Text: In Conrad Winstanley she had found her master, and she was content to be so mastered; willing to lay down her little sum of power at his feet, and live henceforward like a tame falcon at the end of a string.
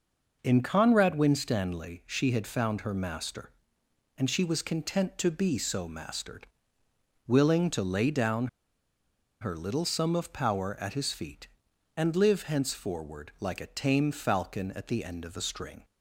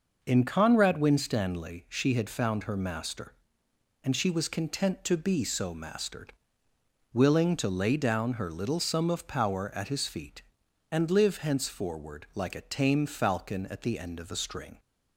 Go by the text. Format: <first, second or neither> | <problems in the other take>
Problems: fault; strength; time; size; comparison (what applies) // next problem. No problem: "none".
second | pauses between "down" and "her"; noticeable; at 8.4 s; 0.94 s long